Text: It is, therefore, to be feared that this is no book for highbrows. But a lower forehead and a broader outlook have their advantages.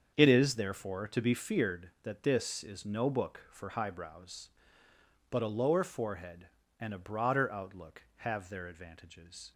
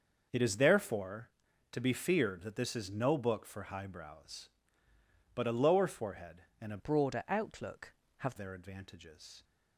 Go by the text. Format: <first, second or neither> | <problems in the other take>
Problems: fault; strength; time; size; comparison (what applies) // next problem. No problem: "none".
first | starts louder than the rest; noticeable; until 1.7 s; 6 dB; also in the first // changes voice from "broader" to "have"; from 6.7 to 8.3 s; 1.6 s long